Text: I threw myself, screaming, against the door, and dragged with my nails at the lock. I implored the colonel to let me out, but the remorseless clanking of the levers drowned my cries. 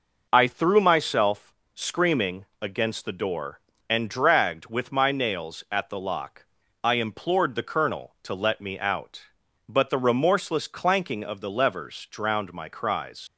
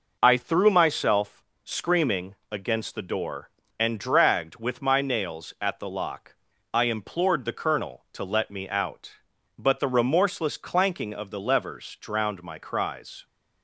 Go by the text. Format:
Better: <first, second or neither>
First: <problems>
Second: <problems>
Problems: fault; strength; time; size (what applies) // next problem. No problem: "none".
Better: second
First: leaves "cries" unfinished; at 13.2 s; 85 ms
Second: none